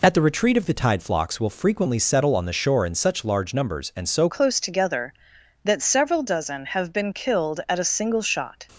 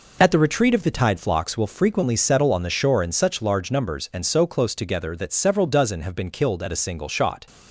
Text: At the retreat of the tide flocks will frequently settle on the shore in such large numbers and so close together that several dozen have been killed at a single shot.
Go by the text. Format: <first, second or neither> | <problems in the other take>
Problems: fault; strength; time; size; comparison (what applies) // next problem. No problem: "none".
second | changes voice at "close"; from 4.2 s on; 4.4 s long